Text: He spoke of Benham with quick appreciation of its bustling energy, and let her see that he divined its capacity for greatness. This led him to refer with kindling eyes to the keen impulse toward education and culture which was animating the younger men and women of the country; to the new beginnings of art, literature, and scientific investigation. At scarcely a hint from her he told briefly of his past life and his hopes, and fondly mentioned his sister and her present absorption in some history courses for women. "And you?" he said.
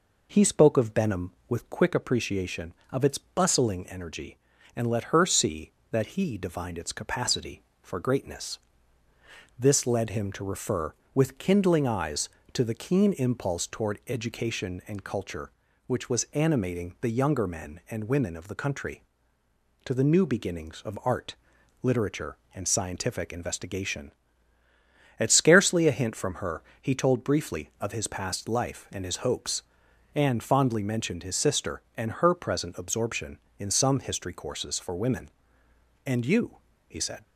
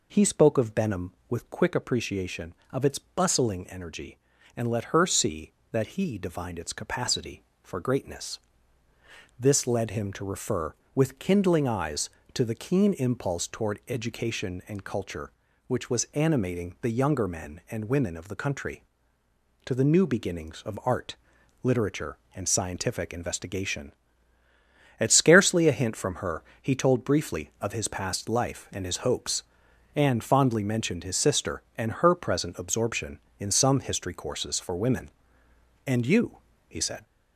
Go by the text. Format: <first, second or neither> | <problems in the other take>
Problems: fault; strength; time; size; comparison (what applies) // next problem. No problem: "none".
first | gets louder; noticeable; throughout; 4 dB // pauses between "her" and "he"; slight; at 26.4 s; 0.18 s long; slight in the first